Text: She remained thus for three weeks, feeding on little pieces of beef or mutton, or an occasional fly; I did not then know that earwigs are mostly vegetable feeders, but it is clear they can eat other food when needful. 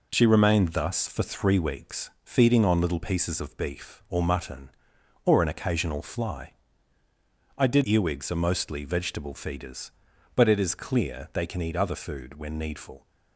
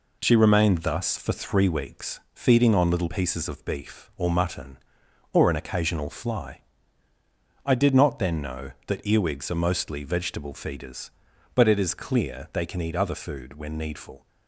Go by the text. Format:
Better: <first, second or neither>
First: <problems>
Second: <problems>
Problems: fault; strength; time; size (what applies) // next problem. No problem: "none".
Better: second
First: skips "not then know that"; at 7.8 s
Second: none